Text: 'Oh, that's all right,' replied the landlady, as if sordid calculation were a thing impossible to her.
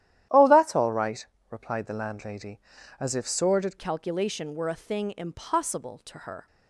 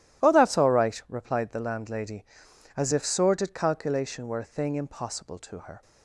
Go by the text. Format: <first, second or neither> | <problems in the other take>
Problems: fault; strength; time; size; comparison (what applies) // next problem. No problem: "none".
second | starts louder than the rest; strong; until 1.5 s; 12 dB // changes voice at "calculation"; from 3.7 s on; 2.7 s long